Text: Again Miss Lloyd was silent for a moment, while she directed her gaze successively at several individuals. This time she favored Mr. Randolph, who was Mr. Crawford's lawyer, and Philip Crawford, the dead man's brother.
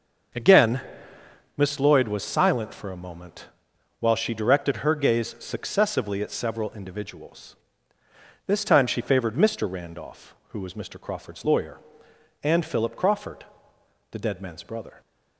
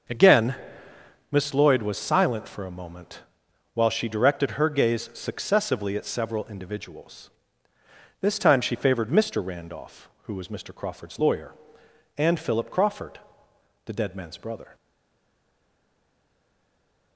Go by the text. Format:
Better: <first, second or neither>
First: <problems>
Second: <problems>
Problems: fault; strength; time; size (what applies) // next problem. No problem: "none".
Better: first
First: starts louder than the rest; until 2.1 s; 6.5 dB // pauses between "Again" and "Miss"; noticeable; at 0.8 s; 0.76 s long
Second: starts louder than the rest; until 1.8 s; 6.5 dB // pauses between "Again" and "Miss"; noticeable; at 0.5 s; 0.76 s long // stays silent after the last word; from 14.7 s on; 2.4 s long